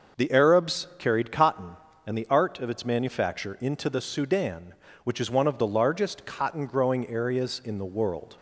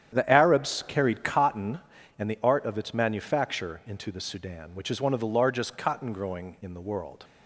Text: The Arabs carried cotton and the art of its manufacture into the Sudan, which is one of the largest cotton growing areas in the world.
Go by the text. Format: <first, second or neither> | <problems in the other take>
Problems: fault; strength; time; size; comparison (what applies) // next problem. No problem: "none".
first | starts louder than the rest; strong; until 1.1 s; 9.5 dB; noticeable in the first // skips "areas"; at 6.5 s